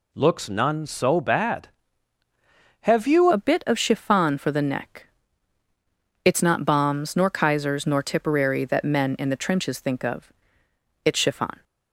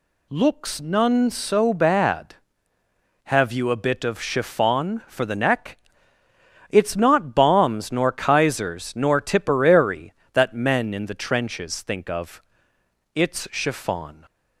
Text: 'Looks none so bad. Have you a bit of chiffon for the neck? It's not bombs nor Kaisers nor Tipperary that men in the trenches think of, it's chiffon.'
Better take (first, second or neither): second